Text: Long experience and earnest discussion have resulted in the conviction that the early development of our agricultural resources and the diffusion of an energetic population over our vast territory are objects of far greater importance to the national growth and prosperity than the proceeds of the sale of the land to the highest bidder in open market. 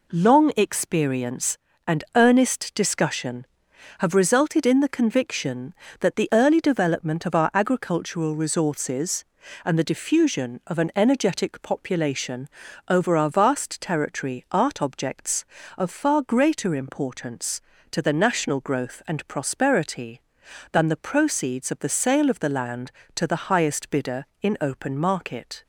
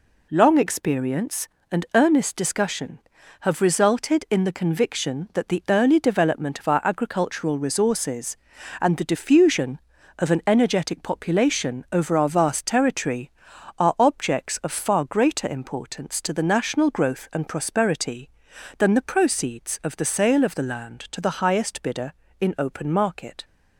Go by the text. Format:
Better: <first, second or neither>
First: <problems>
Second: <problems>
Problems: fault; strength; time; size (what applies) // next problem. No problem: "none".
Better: second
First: pauses between "population" and "over"; at 12.4 s; 0.38 s long // says "art" for "are"; at 14.5 s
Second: none